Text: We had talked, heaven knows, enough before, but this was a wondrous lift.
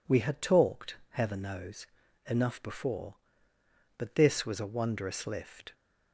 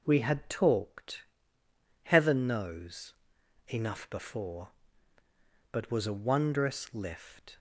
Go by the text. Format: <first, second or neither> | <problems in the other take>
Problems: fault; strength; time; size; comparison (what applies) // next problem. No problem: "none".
first | skips "this"; at 5.9 s